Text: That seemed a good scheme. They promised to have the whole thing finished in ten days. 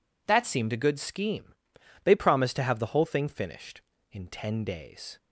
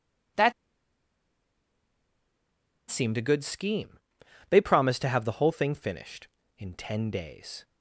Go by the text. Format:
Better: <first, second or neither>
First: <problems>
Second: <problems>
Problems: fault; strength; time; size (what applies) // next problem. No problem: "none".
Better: first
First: none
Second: pauses between "That" and "seemed"; strong; at 0.5 s; 2.3 s long